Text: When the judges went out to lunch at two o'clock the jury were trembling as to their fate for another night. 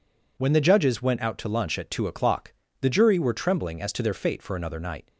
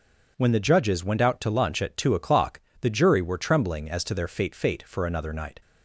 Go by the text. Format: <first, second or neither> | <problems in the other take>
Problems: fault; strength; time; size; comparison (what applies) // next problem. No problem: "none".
first | pauses between "o'clock" and "the"; slight; at 2.5 s; 0.22 s long; slight in the first // says "fate" twice; at 4.5 s